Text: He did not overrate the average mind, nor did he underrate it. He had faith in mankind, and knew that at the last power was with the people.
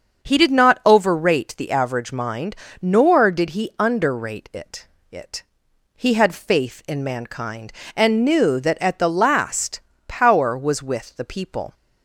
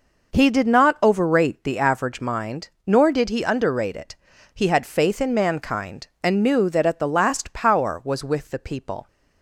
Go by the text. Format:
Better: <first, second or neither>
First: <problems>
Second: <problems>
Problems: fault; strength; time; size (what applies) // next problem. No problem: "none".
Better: second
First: starts louder than the rest; until 1.3 s; 7 dB // says "it" twice; at 5.0 s // pauses between "last" and "power"; slight; at 9.8 s; 0.24 s long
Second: none